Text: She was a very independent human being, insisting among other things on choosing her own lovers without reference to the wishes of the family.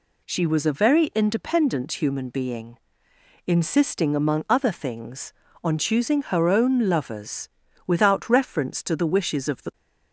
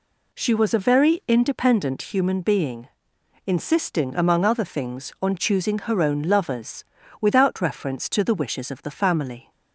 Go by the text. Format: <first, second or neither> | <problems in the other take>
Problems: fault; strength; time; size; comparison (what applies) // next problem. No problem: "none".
second | pauses between "lovers" and "without"; at 7.4 s; 0.38 s long; slight in the second // stops before "family"; at 9.7 s